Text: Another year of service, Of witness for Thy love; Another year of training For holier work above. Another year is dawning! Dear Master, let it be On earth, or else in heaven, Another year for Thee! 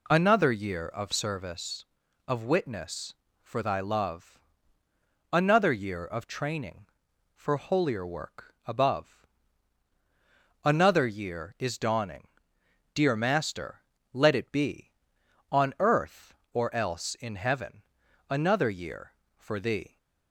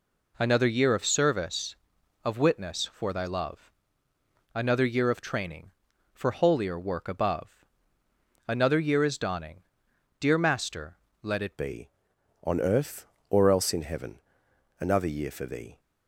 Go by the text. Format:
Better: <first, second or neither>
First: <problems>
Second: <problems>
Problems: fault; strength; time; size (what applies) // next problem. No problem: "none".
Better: first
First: none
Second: changes voice at "be"; from 11.5 s on; 4.2 s long